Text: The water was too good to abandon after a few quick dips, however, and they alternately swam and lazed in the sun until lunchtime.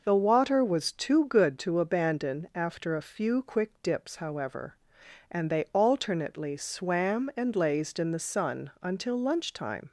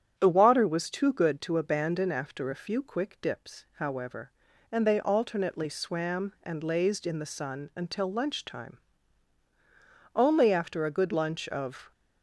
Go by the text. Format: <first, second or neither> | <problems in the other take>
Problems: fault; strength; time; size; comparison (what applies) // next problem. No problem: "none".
first | starts louder than the rest; strong; until 1.1 s; 8.5 dB // goes on to say "Only after a good lunch of"; strong; from 10.1 s on; 1.7 s long